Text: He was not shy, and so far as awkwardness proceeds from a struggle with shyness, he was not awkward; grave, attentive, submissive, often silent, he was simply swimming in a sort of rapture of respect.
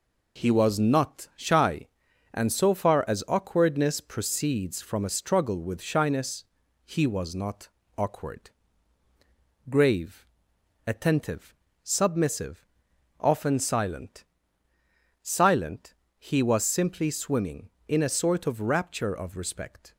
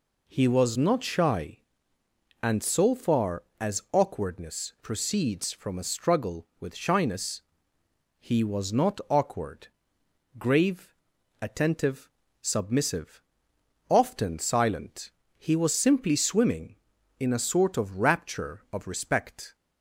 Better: second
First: pauses between "not" and "awkward"; slight; at 7.6 s; 0.28 s long // says "silent" twice; at 15.2 s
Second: none

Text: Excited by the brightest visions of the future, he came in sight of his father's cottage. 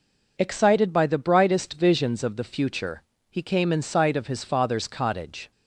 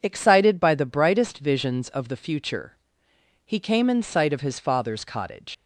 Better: first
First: none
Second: leaves "cottage" unfinished; at 5.5 s; 115 ms

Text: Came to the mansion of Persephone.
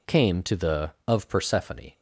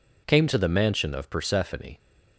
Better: second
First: skips "mansion"; at 0.9 s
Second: none

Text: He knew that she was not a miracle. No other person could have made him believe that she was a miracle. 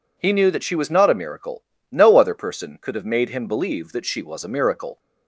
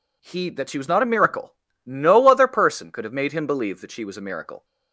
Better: first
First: none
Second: skips "knew"; at 0.5 s

